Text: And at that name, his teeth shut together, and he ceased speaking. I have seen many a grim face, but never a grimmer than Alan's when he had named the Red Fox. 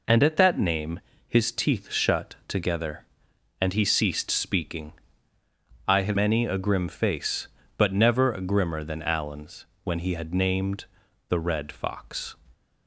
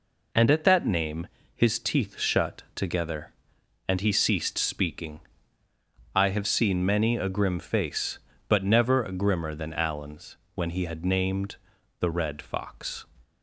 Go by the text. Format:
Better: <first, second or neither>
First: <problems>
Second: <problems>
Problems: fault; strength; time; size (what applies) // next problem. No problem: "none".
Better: second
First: skips "seen"; at 6.1 s // pauses between "Alan's" and "when"; slight; at 9.6 s; 0.18 s long // pauses between "named" and "the"; at 10.8 s; 0.44 s long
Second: pauses between "Alan's" and "when"; slight; at 10.3 s; 0.18 s long // pauses between "named" and "the"; at 11.5 s; 0.44 s long